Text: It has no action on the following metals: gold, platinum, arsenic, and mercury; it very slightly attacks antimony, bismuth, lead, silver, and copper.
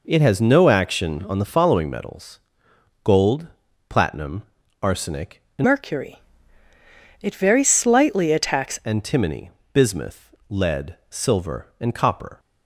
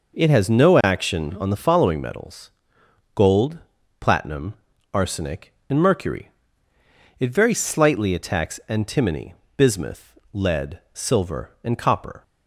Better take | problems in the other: second | changes voice from "mercury" to "attacks"; from 5.6 to 8.7 s; 3.1 s long

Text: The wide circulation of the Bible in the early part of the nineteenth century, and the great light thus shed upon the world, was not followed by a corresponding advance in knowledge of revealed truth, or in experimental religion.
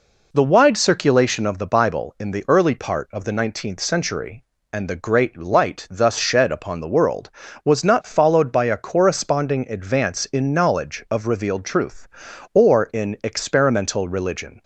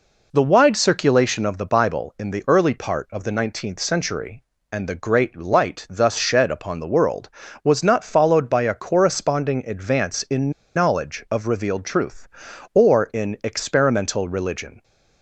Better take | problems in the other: first | pauses between "in" and "knowledge"; slight; at 10.5 s; 0.23 s long

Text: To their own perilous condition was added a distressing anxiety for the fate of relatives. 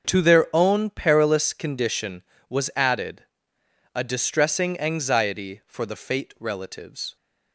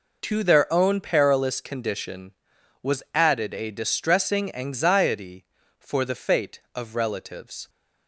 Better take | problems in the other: second | starts louder than the rest; until 1.1 s; 7 dB // pauses between "added" and "a"; noticeable; at 3.2 s; 0.72 s long // skips "of"; at 6.3 s

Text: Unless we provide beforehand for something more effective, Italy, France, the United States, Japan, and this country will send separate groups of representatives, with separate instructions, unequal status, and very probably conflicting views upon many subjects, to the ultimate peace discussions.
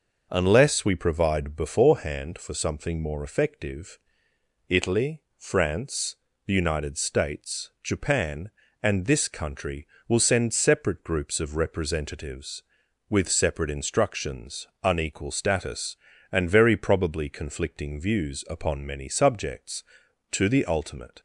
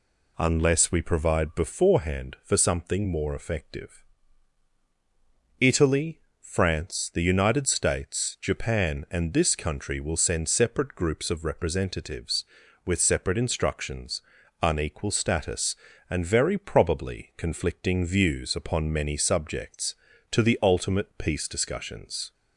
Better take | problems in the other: second | stops before "peace discussions"; at 21.1 s

